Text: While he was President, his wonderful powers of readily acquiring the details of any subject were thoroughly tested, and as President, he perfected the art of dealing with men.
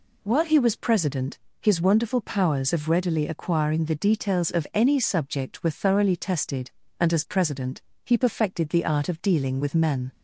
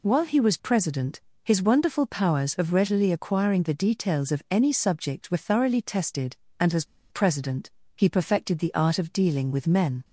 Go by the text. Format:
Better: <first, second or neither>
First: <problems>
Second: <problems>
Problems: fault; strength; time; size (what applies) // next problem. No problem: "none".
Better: first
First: none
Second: pauses between "as" and "President"; slight; at 6.8 s; 0.25 s long